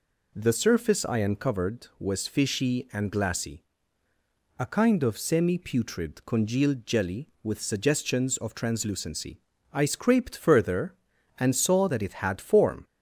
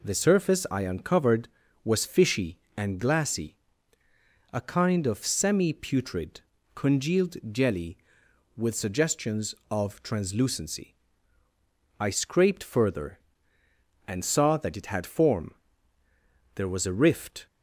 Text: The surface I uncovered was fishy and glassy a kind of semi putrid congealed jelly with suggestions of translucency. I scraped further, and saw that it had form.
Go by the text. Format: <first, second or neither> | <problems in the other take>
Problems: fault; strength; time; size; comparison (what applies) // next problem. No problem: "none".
first | pauses between "glassy" and "a"; noticeable; at 3.5 s; 0.94 s long; noticeable in the first // pauses between "putrid" and "congealed"; slight; at 6.4 s; 0.34 s long // pauses between "congealed" and "jelly"; slight; at 7.3 s; 0.16 s long // goes on to say "There was a rift"; noticeable; from 16.5 s on; 0.92 s long